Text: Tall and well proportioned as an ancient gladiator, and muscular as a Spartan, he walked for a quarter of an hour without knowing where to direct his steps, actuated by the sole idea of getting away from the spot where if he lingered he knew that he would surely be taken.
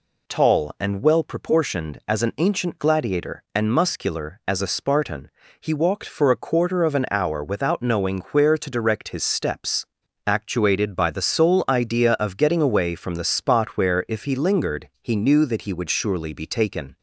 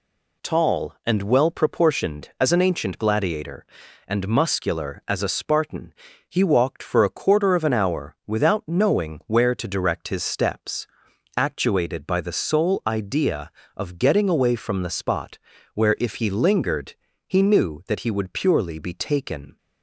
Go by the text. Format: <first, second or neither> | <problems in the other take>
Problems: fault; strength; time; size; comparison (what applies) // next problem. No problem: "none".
first | pauses between "spot" and "where"; at 15.3 s; 0.38 s long // pauses between "lingered" and "he"; slight; at 16.9 s; 0.32 s long // says "purely" for "surely"; at 18.3 s